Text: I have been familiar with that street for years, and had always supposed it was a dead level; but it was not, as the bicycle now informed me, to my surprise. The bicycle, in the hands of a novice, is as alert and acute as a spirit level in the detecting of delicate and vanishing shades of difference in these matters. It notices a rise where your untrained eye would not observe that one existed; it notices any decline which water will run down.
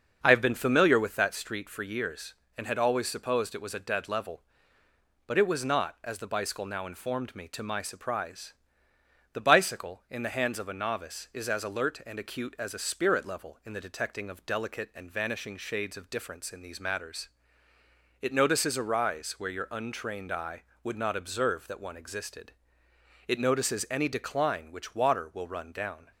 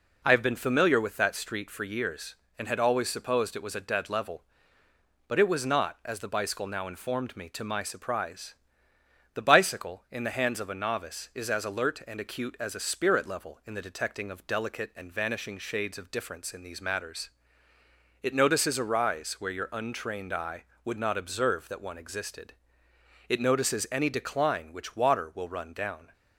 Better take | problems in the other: second | starts louder than the rest; until 1.2 s; 6.5 dB

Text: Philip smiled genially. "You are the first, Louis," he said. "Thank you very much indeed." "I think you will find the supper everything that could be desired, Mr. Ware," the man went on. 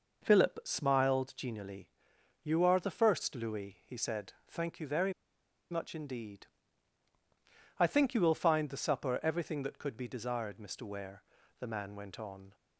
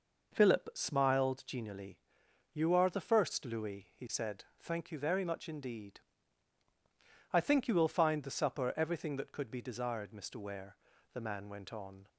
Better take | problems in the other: second | pauses between "very" and "much"; noticeable; at 5.1 s; 0.58 s long

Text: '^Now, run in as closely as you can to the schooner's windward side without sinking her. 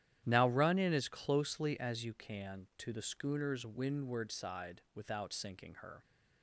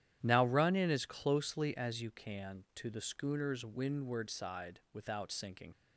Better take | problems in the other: first | starts louder than the rest; strong; until 1.2 s; 10.5 dB; strong in the first // stops before "her"; at 5.7 s

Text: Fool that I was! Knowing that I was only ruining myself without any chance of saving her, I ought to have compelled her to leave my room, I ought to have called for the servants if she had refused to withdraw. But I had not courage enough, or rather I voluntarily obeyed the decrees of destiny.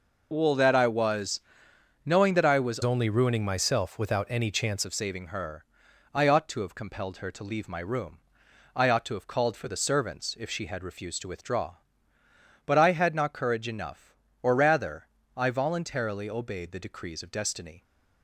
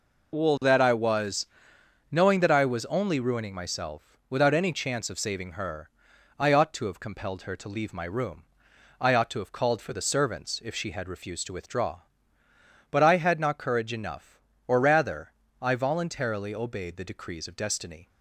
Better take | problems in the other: second | changes voice from "only" to "chance"; from 2.8 to 4.8 s; 2.0 s long // pauses between "rather" and "I"; slight; at 15.0 s; 0.28 s long; slight in the second

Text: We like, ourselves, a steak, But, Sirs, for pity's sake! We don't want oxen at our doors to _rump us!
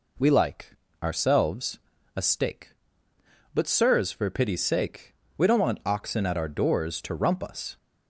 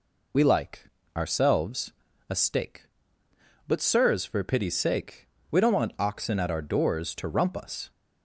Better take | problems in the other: first | loses the start of "We"; at 0.3 s; 45 ms

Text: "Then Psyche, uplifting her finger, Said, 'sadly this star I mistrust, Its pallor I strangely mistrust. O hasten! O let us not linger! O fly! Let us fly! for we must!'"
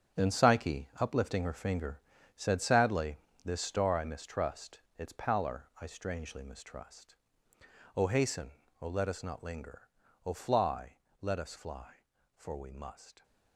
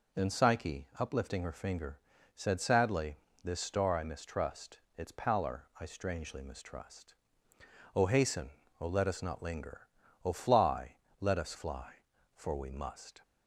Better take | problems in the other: second | gets quieter; strong; throughout; 10.5 dB // pauses between "sadly" and "this"; slight; at 3.1 s; 0.26 s long; slight in the second

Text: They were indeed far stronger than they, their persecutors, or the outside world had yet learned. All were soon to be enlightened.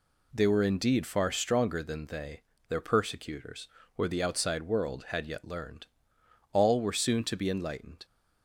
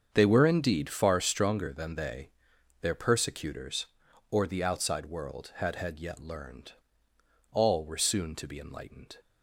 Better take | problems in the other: first | starts louder than the rest; until 1.1 s; 7 dB // says "had" twice; at 5.7 s

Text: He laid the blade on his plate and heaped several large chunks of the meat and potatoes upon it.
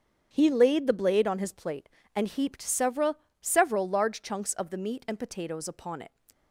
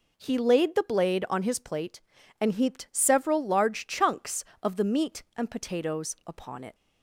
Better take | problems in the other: second | starts louder than the rest; strong; until 1.3 s; 8 dB // says "several" twice; at 3.4 s

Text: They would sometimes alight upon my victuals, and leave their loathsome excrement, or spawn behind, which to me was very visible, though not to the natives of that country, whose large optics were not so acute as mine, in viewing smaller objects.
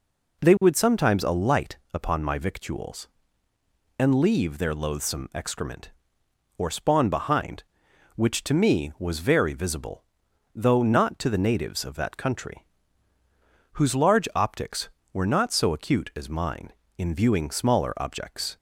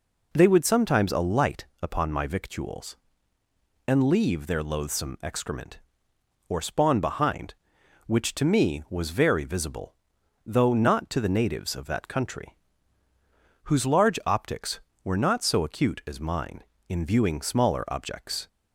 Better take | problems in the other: neither | pauses between "alight" and "upon"; slight; the same in both

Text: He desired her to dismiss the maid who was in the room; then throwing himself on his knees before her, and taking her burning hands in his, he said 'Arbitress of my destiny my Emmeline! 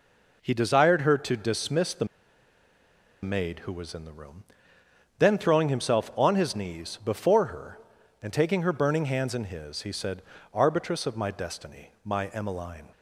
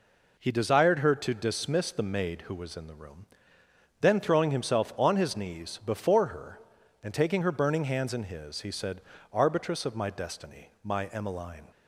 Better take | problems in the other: second | pauses between "the" and "maid"; at 2.0 s; 1.1 s long // pauses between "said" and "Arbitress"; slight; at 10.2 s; 0.32 s long; slight in the second

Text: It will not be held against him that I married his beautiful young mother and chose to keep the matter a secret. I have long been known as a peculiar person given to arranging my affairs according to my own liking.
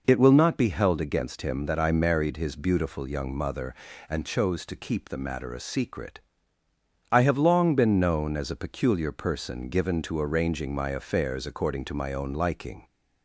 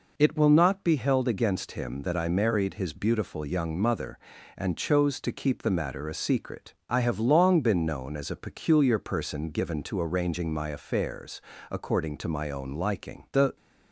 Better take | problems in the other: first | pauses between "affairs" and "according"; slight; at 11.4 s; 0.28 s long // goes on to say "The"; slight; from 13.3 s on; 0.22 s long

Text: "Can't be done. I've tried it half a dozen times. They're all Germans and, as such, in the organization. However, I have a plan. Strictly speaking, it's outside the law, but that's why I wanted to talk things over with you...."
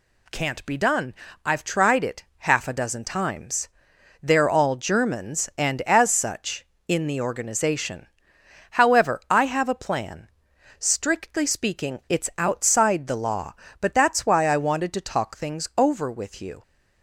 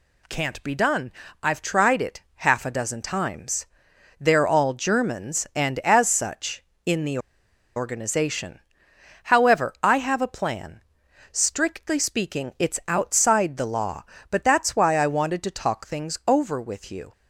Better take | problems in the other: first | pauses between "the" and "organization"; noticeable; at 7.1 s; 0.57 s long

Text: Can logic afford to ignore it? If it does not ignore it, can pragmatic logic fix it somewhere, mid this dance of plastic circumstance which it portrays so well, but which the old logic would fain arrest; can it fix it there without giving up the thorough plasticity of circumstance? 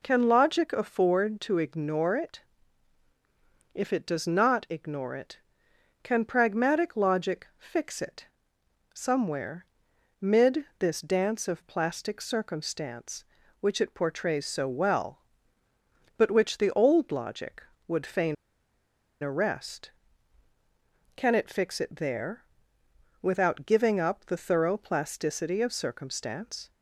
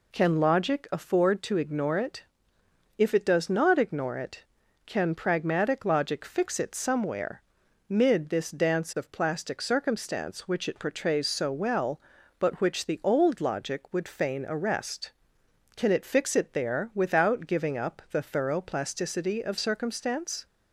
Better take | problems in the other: second | pauses between "it" and "somewhere"; noticeable; at 8.2 s; 0.68 s long // pauses between "fain" and "arrest"; noticeable; at 18.3 s; 0.87 s long // pauses between "there" and "without"; noticeable; at 22.4 s; 0.76 s long

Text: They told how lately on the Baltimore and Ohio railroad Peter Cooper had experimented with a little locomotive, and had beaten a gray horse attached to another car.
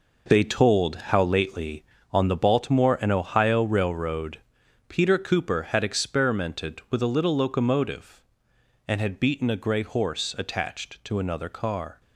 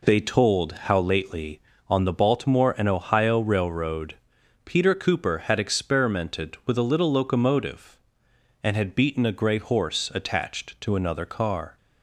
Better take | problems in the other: second | gets quieter; strong; throughout; 9 dB // pauses between "railroad" and "Peter"; noticeable; at 4.3 s; 0.50 s long; noticeable in the second

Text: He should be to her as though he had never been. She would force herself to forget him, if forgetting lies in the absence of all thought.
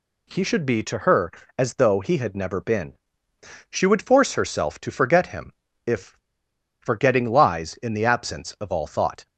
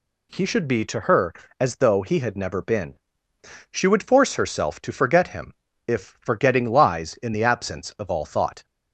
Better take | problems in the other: second | pauses between "if" and "forgetting"; noticeable; at 6.1 s; 0.63 s long

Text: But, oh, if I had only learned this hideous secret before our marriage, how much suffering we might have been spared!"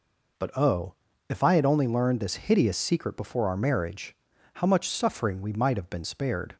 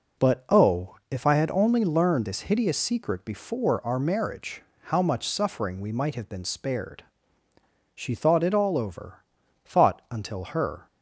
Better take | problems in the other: first | goes on to say "She thought it all over thought until her"; strong; from 7.9 s on; 2.9 s long

